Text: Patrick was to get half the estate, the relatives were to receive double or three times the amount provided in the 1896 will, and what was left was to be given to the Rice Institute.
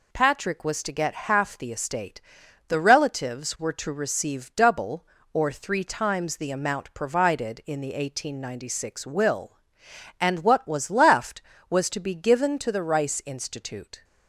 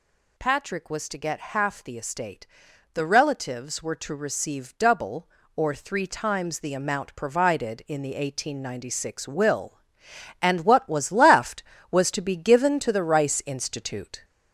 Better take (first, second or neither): first